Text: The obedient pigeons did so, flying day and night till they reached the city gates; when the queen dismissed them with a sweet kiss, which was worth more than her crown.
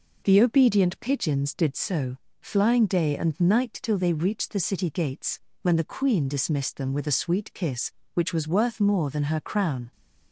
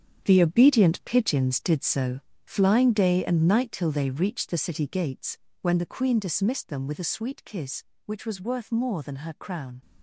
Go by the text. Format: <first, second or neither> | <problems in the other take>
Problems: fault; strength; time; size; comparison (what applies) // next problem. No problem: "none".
first | gets quieter; strong; throughout; 11 dB